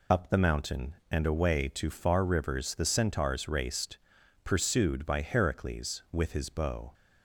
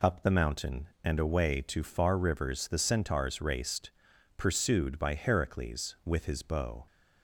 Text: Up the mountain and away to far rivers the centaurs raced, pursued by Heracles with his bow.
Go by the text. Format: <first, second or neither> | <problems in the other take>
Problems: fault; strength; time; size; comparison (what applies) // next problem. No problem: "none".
second | loses the start of "Up"; at 0.1 s; 20 ms